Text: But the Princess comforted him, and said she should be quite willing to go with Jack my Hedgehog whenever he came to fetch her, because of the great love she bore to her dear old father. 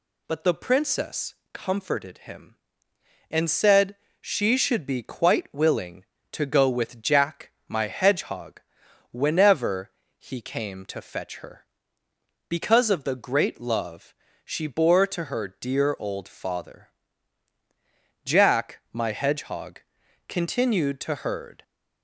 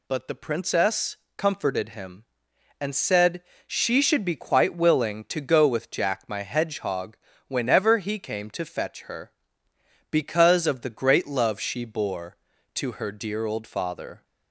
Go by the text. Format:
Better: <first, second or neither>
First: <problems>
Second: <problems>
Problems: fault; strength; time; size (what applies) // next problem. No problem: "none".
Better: second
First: pauses between "Princess" and "comforted"; slight; at 1.3 s; 0.18 s long // pauses between "said" and "she"; slight; at 3.9 s; 0.26 s long // pauses between "Jack" and "my"; slight; at 7.5 s; 0.16 s long // pauses between "Hedgehog" and "whenever"; noticeable; at 8.6 s; 0.50 s long // pauses between "whenever" and "he"; slight; at 9.9 s; 0.26 s long // pauses between "love" and "she"; slight; at 14.1 s; 0.30 s long // goes on to say "Jack my Hedgehog continued to herd"; strong; from 18.2 s on; 3.3 s long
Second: pauses between "Princess" and "comforted"; slight; at 1.1 s; 0.20 s long // pauses between "said" and "she"; slight; at 3.4 s; 0.24 s long // pauses between "Hedgehog" and "whenever"; slight; at 7.1 s; 0.32 s long